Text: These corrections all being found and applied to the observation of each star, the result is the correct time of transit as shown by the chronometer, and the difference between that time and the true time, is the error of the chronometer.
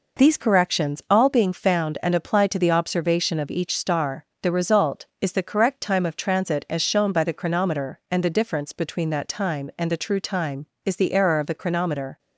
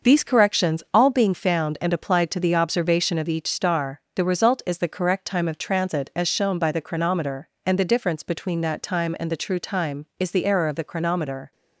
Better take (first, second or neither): first